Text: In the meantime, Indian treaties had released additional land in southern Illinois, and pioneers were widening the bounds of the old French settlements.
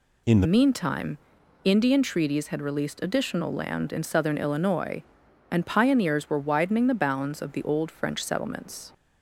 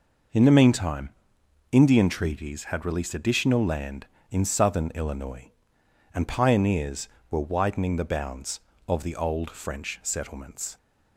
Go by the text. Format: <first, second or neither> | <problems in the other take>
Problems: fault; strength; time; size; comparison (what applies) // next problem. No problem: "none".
second | changes voice at "meantime"; from 0.4 s on; 8.5 s long